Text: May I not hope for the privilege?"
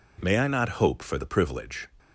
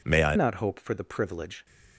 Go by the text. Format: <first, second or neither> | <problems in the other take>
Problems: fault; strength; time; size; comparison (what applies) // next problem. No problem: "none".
first | changes voice at "not"; from 0.3 s on; 1.3 s long